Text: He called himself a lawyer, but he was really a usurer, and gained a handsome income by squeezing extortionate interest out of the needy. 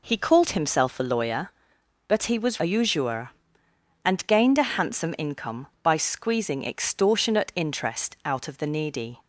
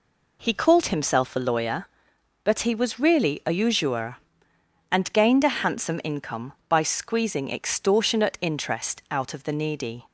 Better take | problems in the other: second | skips "really"; at 2.5 s

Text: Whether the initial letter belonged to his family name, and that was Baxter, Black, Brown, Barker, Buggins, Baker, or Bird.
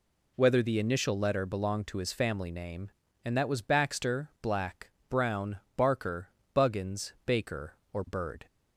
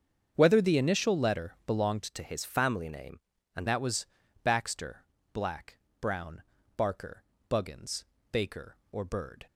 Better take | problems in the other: first | starts louder than the rest; strong; until 1.3 s; 7.5 dB // changes voice from "to" to "and"; from 2.0 to 3.6 s; 1.6 s long // pauses between "was" and "Baxter"; slight; at 4.0 s; 0.36 s long

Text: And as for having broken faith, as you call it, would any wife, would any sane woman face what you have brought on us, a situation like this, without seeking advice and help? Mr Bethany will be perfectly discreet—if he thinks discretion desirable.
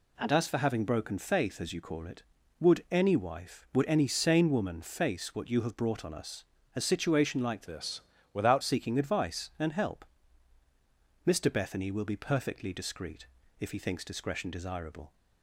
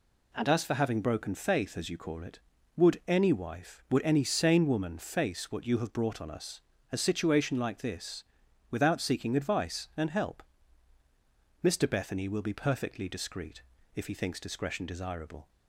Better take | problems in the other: second | changes voice from "this" to "without"; from 7.6 to 8.6 s; 1.0 s long

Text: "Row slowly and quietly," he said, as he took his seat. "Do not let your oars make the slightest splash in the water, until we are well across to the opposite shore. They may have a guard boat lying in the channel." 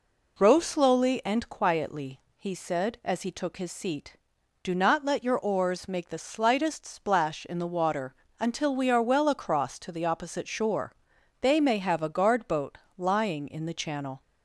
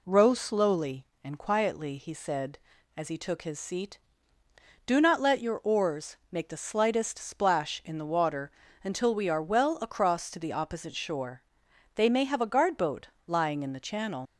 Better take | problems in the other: first | pauses between "boat" and "lying"; slight; at 13.0 s; 0.18 s long; slight in the first // leaves "channel" unfinished; at 14.2 s; 85 ms

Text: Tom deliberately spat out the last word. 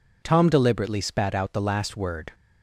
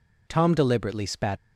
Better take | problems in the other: first | stops before "out the last word"; at 1.3 s

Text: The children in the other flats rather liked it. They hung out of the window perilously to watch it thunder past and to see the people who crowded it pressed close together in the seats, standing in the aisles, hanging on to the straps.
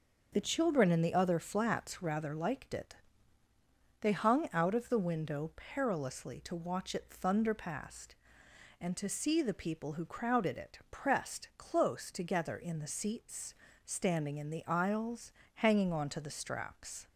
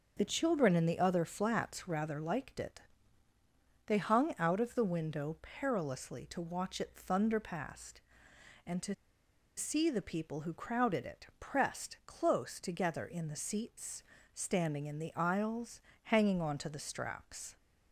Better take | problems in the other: first | starts louder than the rest; until 1.1 s; 6 dB; also in the first // pauses between "to" and "see"; noticeable; at 8.9 s; 0.63 s long

